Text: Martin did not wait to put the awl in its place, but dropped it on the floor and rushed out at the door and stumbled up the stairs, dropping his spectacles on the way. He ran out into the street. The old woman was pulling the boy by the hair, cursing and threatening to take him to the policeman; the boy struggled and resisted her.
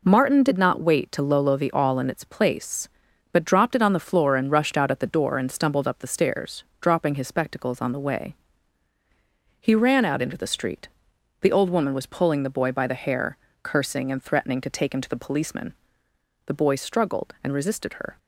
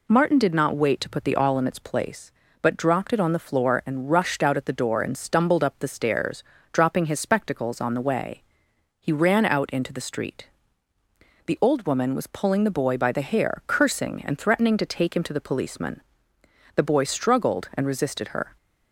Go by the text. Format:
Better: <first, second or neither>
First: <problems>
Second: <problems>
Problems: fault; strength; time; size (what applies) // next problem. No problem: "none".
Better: second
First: says "lolo" for "put"; at 1.2 s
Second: none